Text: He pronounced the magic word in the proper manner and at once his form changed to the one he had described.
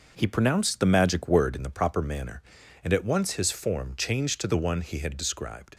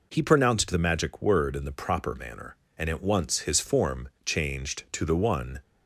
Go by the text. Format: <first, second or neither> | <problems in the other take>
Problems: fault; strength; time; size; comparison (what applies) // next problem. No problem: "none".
first | pauses between "form" and "changed"; slight; at 4.0 s; 0.16 s long // stops before "he had described"; at 5.6 s